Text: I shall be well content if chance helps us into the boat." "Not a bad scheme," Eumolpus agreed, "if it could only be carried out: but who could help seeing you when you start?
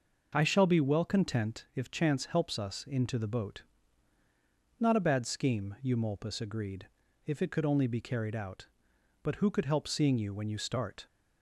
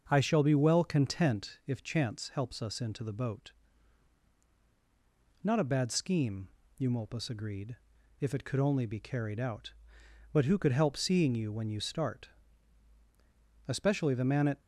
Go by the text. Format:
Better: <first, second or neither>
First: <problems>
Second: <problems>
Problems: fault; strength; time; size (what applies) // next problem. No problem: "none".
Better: first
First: none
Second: starts louder than the rest; noticeable; until 1.0 s; 6 dB // goes on to say "Especially the man at"; noticeable; from 13.6 s on; 0.92 s long